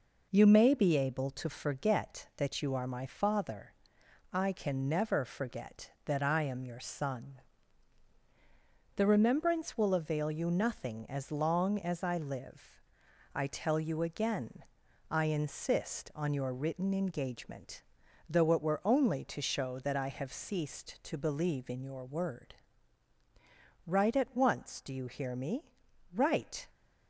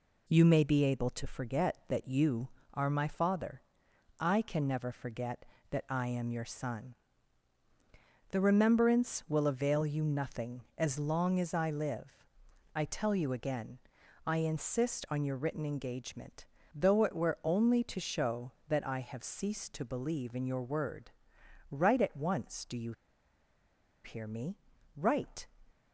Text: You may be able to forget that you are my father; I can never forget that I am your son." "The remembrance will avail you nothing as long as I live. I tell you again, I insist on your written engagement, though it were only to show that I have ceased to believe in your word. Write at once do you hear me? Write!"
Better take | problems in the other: first | pauses between "you" and "hear"; at 22.9 s; 1.1 s long

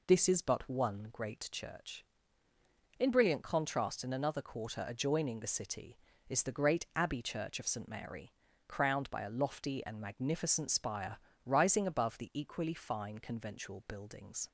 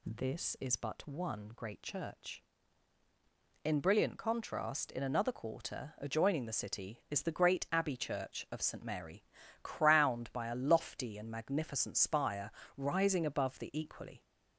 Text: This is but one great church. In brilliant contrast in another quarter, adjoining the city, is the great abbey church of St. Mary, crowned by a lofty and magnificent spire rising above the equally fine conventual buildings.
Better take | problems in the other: first | pauses between "spire" and "rising"; slight; at 12.4 s; 0.26 s long; slight in the first // stops before "fine conventual buildings"; at 14.2 s

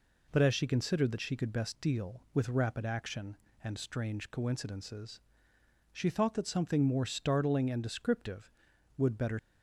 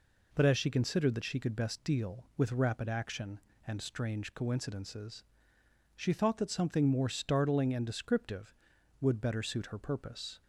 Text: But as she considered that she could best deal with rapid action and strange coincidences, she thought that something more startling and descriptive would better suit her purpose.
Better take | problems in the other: second | stops before "suit her purpose"; at 9.3 s

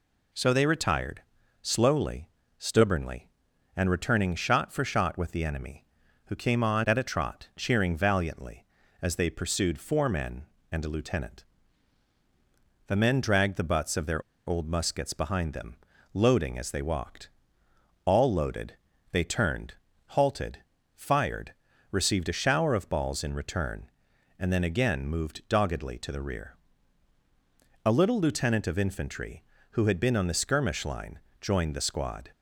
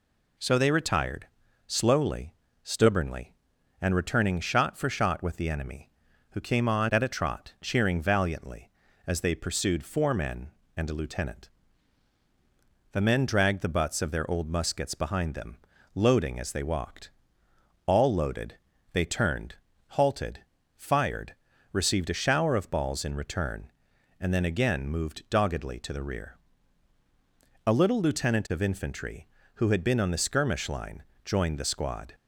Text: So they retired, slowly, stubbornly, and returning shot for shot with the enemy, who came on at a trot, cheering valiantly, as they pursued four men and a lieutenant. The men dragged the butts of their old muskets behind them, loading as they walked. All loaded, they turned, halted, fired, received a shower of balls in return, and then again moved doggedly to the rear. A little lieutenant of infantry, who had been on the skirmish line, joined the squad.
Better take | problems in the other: second | pauses between "their" and "old"; slight; at 14.2 s; 0.25 s long

